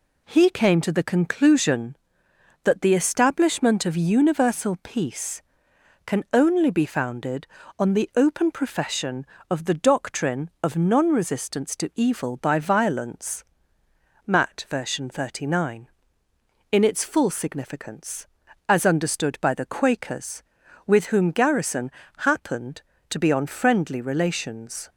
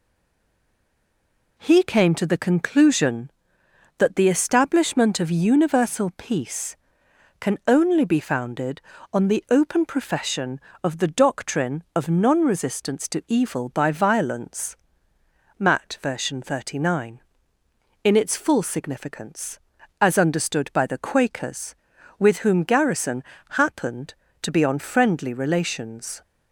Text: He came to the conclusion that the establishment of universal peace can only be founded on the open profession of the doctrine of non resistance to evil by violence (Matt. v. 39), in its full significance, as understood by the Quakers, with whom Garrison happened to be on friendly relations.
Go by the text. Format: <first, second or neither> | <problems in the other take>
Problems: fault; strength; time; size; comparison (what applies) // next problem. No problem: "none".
first | stays silent before the first word; noticeable; until 1.5 s; 1.5 s long // pauses between "Garrison" and "happened"; slight; at 23.2 s; 0.28 s long; slight in the first